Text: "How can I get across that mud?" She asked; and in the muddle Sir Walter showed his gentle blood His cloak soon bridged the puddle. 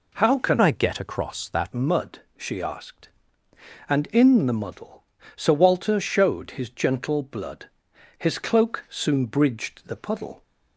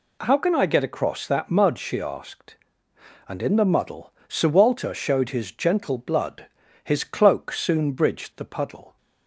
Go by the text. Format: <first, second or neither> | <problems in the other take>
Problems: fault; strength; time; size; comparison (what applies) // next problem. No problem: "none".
second | changes voice from "I" to "that"; from 0.6 to 1.7 s; 1.1 s long // pauses between "muddle" and "Sir"; slight; at 5.0 s; 0.32 s long; slight in the second // pauses between "blood" and "His"; noticeable; at 7.6 s; 0.50 s long; also in the second